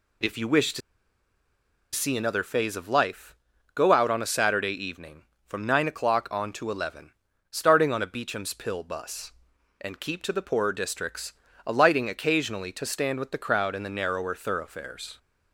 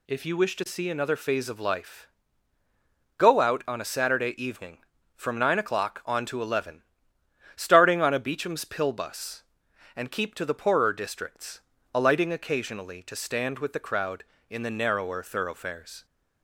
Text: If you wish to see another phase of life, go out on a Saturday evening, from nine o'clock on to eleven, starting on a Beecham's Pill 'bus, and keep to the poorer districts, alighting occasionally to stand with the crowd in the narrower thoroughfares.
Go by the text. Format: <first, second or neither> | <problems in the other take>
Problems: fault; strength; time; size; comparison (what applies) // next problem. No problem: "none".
second | pauses between "to" and "see"; at 0.8 s; 1.1 s long